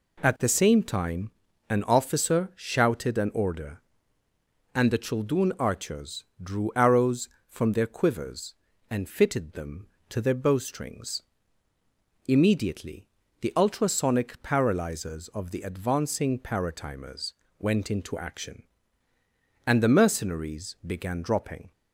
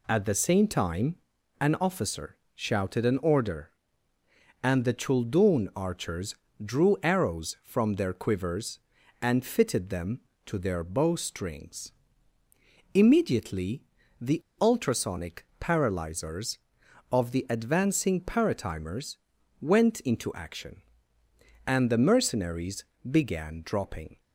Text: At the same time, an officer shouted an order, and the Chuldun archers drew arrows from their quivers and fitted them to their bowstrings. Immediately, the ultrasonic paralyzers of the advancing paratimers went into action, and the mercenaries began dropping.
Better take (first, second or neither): first